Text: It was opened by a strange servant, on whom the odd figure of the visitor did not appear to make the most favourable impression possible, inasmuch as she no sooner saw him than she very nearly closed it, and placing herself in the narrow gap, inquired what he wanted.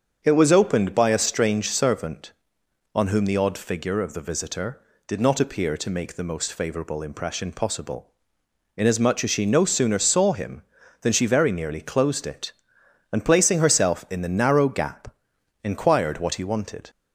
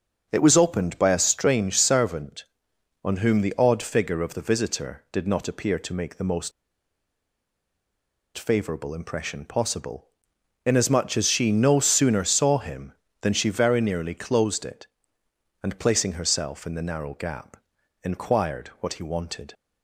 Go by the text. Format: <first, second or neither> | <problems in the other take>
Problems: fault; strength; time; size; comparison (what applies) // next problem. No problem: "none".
first | starts louder than the rest; until 1.3 s; 6.5 dB; also in the first // pauses between "most" and "favourable"; strong; at 6.5 s; 1.8 s long